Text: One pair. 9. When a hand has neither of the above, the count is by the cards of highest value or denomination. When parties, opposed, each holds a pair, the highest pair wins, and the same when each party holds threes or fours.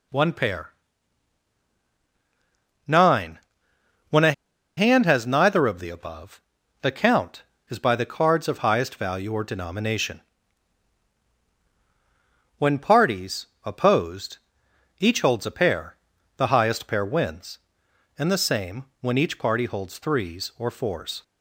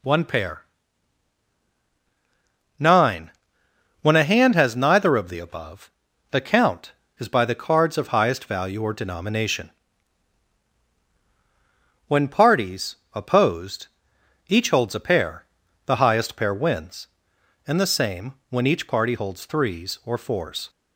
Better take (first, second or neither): second